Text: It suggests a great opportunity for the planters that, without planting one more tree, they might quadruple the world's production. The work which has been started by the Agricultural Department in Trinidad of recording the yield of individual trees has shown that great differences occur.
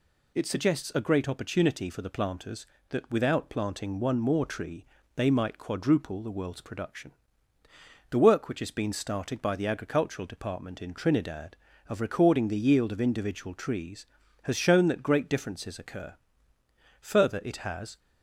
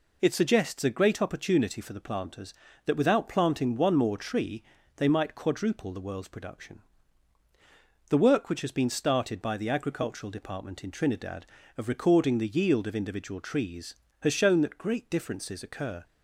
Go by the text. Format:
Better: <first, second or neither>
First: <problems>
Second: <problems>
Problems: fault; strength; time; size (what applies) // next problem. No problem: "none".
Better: second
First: goes on to say "Further it has"; noticeable; from 17.0 s on; 0.98 s long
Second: none